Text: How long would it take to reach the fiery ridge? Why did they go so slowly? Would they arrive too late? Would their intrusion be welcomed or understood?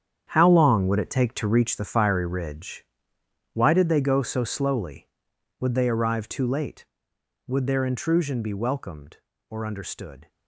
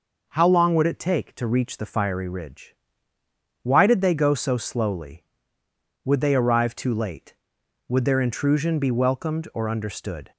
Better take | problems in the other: second | gets quieter; strong; throughout; 12 dB

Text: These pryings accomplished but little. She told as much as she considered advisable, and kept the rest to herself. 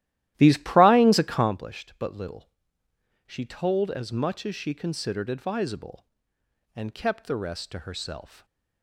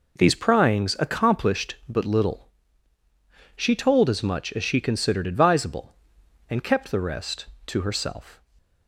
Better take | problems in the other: second | starts louder than the rest; strong; until 1.6 s; 14 dB

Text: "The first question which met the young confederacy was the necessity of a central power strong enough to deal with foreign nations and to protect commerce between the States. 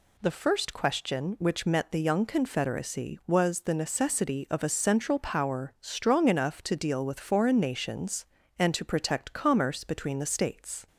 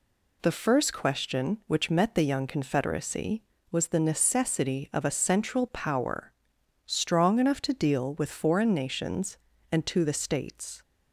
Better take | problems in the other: first | pauses between "power" and "strong"; noticeable; at 6.3 s; 0.54 s long // skips "protect commerce between"; at 10.0 s

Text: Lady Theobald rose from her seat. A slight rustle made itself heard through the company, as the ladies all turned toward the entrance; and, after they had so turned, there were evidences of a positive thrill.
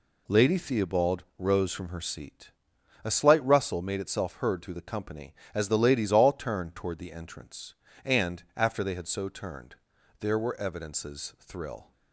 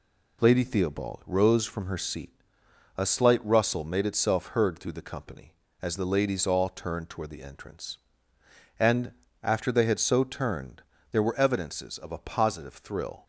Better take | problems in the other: second | pauses between "Theobald" and "rose"; slight; at 1.2 s; 0.16 s long // skips "of a positive"; at 11.3 s

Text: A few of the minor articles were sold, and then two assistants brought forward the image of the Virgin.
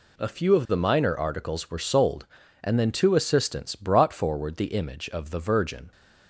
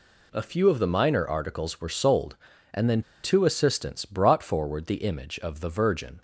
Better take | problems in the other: first | pauses between "then" and "two"; slight; at 3.0 s; 0.22 s long

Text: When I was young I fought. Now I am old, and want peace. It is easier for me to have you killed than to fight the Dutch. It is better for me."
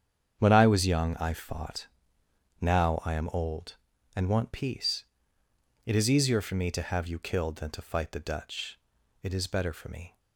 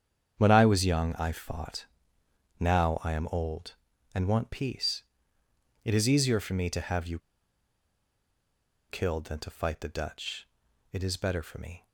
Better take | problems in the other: first | starts louder than the rest; strong; until 1.3 s; 8 dB; strong in the first // pauses between "you" and "killed"; strong; at 7.1 s; 1.7 s long

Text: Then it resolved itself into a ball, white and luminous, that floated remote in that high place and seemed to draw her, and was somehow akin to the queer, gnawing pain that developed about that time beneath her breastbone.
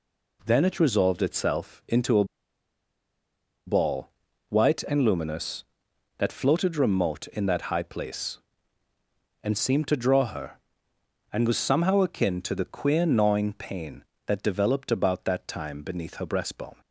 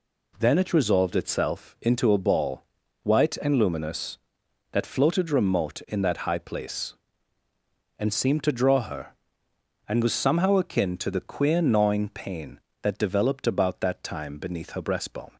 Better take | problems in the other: second | pauses between "a" and "ball"; strong; at 2.2 s; 1.4 s long

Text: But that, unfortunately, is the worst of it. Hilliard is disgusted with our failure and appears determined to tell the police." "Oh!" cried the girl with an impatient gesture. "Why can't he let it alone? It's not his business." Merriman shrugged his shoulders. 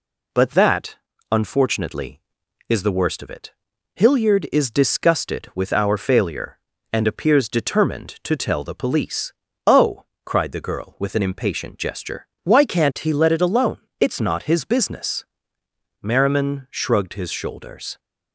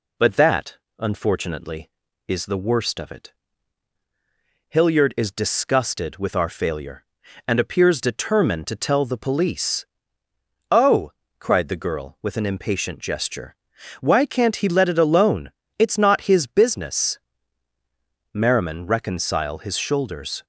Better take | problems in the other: first | says "reconcile" for "shrugged"; at 18.8 s

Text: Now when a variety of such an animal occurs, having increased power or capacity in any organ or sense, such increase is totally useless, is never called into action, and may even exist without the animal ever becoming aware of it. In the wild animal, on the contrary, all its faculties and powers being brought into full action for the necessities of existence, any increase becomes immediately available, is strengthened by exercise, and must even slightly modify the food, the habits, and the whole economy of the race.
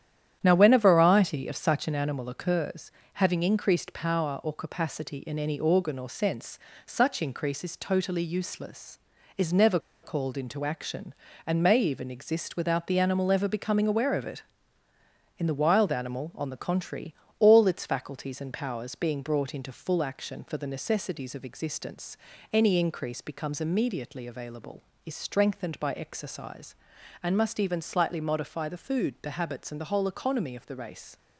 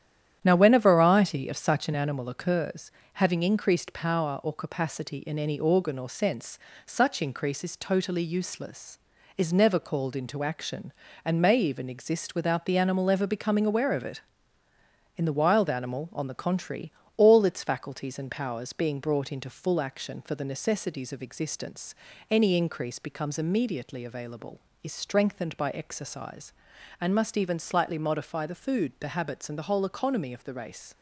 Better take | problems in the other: second | starts louder than the rest; strong; until 1.4 s; 10 dB; strong in the second // pauses between "never" and "called"; slight; at 9.8 s; 0.21 s long

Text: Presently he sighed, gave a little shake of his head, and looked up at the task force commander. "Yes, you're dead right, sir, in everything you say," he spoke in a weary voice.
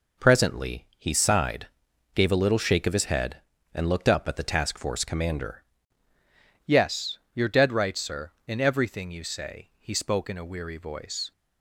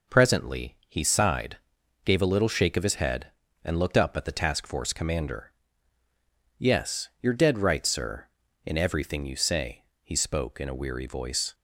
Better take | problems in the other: second | changes voice at "Yes"; from 6.6 s on; 4.7 s long

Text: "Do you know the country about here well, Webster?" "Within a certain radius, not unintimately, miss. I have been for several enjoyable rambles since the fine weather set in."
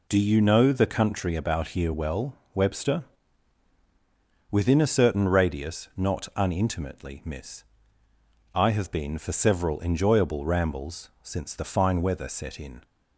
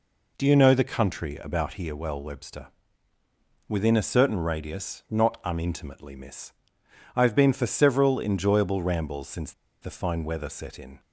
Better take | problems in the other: first | pauses between "since" and "the"; slight; at 9.5 s; 0.28 s long

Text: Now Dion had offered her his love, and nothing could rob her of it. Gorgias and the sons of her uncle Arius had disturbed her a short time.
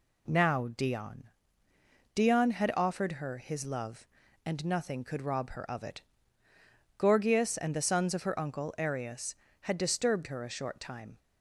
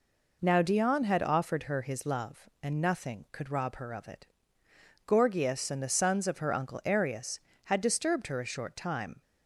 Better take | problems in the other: second | says "Dion" twice; at 2.1 s

